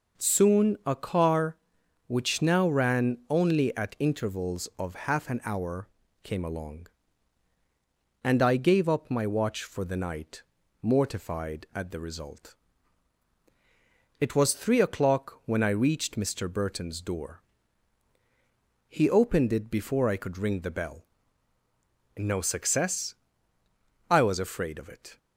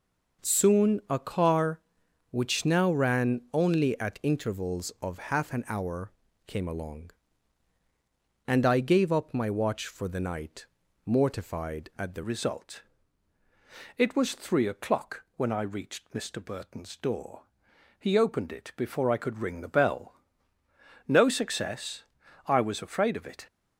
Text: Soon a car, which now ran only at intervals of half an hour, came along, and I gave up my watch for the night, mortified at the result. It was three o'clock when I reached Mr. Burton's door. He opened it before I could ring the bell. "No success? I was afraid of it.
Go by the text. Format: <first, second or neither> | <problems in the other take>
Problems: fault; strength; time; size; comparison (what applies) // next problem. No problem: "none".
first | changes voice at "result"; from 12.2 s on; 11.2 s long